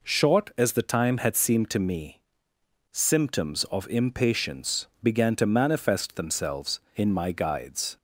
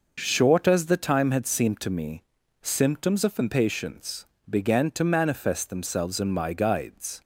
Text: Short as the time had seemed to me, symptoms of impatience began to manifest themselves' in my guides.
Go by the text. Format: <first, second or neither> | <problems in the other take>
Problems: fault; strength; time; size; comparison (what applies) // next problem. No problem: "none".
neither | pauses between "impatience" and "began"; slight; the same in both